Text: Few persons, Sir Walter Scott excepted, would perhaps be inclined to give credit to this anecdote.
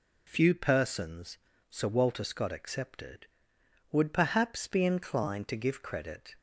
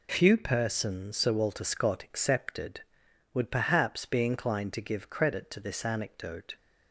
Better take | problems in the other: second | stops before "to this anecdote"; at 6.3 s

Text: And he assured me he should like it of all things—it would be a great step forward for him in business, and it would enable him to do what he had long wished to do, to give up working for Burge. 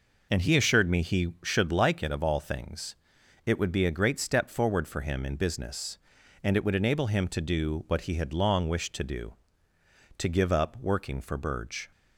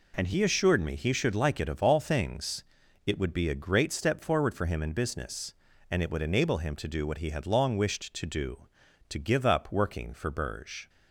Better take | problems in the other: neither | none

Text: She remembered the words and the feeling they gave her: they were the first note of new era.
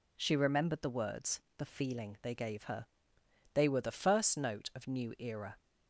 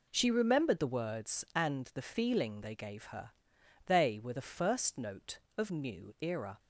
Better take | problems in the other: second | skips "and"; at 1.4 s

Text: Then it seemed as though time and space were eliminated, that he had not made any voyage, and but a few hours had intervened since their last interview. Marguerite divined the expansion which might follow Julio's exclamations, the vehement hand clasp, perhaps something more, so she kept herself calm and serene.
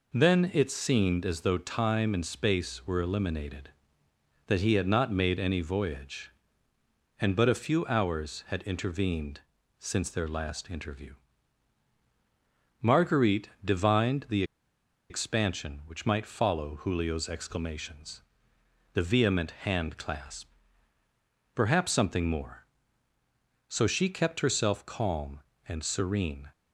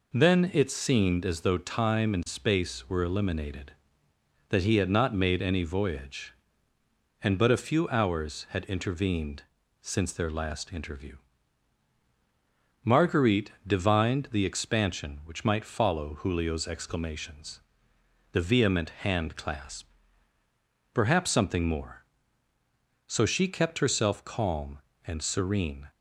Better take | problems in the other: second | pauses between "intervened" and "since"; slight; at 9.4 s; 0.36 s long; slight in the second // pauses between "the" and "expansion"; noticeable; at 14.4 s; 0.66 s long

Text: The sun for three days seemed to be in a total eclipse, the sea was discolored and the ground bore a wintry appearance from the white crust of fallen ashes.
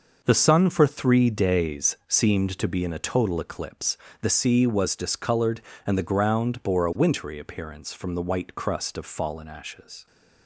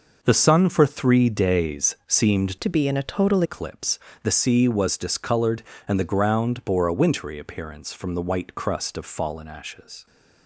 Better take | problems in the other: first | changes voice from "to" to "total"; from 2.5 to 3.4 s; 0.9 s long

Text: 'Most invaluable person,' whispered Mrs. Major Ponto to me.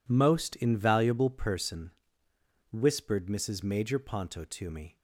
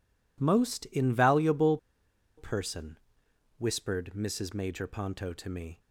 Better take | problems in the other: first | pauses between "invaluable" and "person"; noticeable; at 1.7 s; 0.60 s long

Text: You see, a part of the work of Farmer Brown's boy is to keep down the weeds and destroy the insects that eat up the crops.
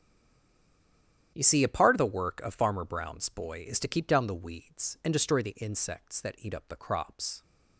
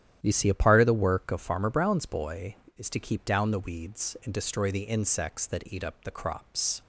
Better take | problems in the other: second | stays silent before the first word; noticeable; until 1.3 s; 1.3 s long // starts louder than the rest; strong; until 2.3 s; 10 dB; strong in the second

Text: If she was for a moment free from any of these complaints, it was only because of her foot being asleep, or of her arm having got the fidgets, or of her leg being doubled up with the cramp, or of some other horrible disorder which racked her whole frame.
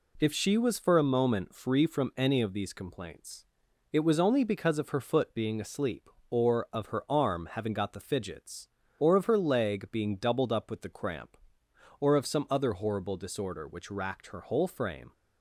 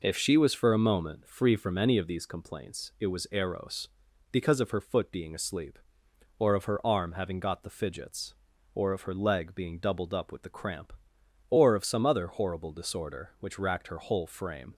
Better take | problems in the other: first | says "eros" for "only"; at 3.3 s

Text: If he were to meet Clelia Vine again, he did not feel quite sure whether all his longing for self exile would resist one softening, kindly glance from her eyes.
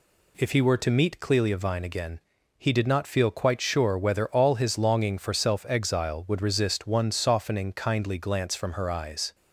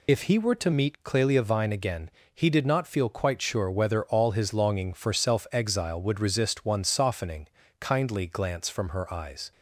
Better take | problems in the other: first | loses the start of "If"; at 0.0 s; 40 ms

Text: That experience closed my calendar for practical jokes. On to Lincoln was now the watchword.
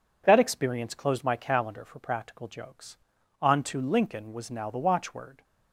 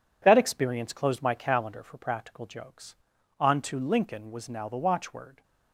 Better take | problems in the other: first | gets quieter; throughout; 7 dB

